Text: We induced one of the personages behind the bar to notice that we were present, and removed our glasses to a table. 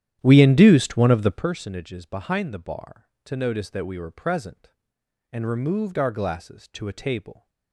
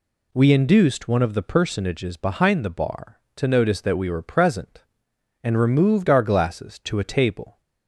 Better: second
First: starts louder than the rest; strong; until 1.4 s; 11 dB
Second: none

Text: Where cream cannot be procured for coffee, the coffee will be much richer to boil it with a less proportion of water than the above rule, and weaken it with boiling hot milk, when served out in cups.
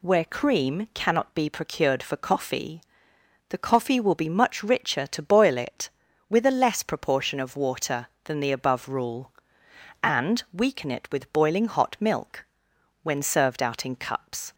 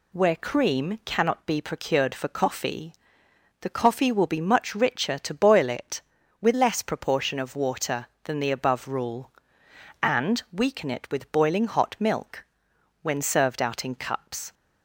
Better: first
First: none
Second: skips "a"; at 6.5 s

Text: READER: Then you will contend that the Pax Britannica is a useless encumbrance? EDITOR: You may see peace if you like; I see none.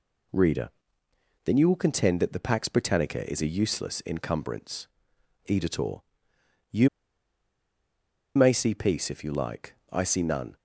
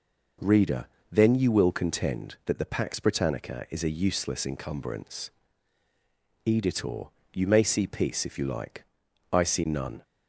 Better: second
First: pauses between "You" and "may"; strong; at 6.8 s; 1.4 s long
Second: none

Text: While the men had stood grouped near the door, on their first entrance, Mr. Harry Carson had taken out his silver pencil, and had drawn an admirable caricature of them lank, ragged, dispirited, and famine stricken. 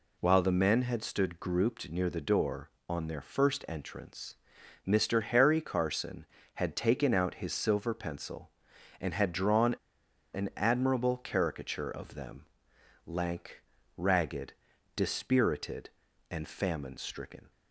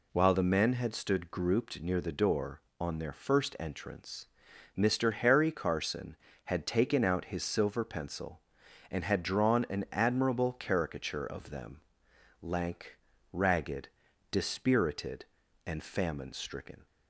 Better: second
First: pauses between "drawn" and "an"; noticeable; at 9.7 s; 0.57 s long // pauses between "them" and "lank"; noticeable; at 12.4 s; 0.58 s long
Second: pauses between "them" and "lank"; noticeable; at 11.8 s; 0.58 s long

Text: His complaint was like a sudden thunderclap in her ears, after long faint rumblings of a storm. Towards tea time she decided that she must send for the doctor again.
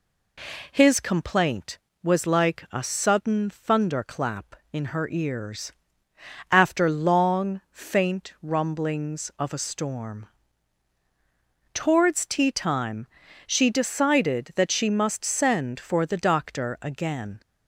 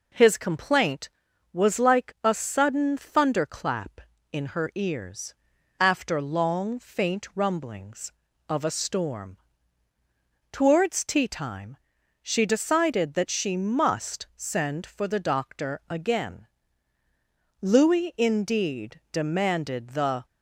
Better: first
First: pauses between "time" and "she"; at 13.0 s; 0.40 s long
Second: pauses between "time" and "she"; at 11.7 s; 0.44 s long // goes on to say "Louis indeed demanded the"; strong; from 17.6 s on; 2.6 s long

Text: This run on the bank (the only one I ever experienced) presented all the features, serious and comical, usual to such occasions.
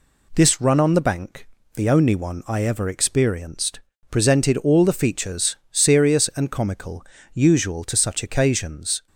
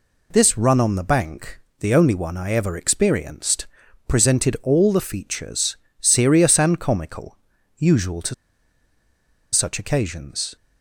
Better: first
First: none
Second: pauses between "to" and "such"; at 8.3 s; 1.1 s long

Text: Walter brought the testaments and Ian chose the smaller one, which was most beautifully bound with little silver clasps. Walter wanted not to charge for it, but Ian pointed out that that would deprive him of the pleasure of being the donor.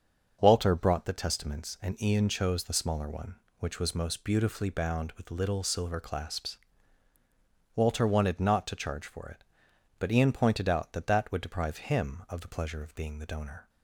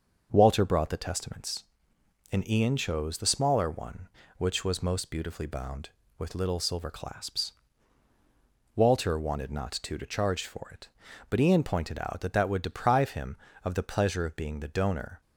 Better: first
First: starts louder than the rest; until 1.4 s; 6.5 dB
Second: starts louder than the rest; until 1.3 s; 6.5 dB // says "to" twice; at 9.9 s

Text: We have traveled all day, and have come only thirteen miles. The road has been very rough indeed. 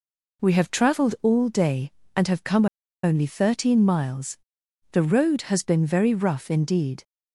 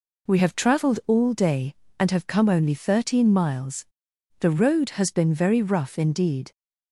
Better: second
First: pauses between "come" and "only"; at 2.6 s; 0.37 s long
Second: none

